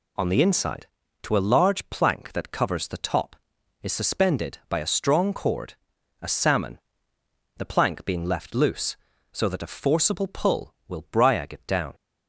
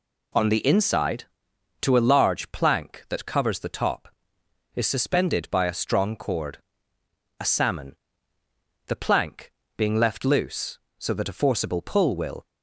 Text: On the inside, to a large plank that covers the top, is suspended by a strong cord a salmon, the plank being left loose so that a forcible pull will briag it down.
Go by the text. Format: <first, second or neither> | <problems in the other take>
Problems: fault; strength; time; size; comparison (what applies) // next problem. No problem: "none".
first | pauses between "cord" and "a"; noticeable; at 6.5 s; 0.82 s long; noticeable in the first // pauses between "plank" and "being"; slight; at 9.5 s; 0.26 s long // stops before "briag it down"; at 12.4 s